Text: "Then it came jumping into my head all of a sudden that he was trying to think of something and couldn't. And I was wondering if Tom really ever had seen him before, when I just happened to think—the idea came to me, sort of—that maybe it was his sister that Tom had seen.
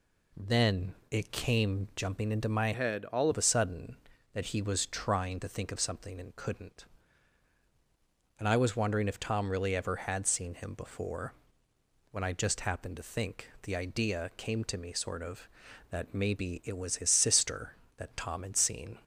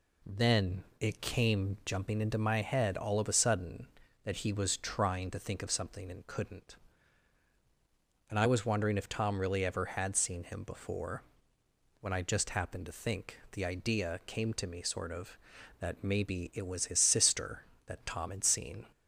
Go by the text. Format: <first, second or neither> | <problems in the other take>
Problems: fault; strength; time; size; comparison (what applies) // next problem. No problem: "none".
second | changes voice from "head" to "all"; from 2.7 to 3.2 s; 0.5 s long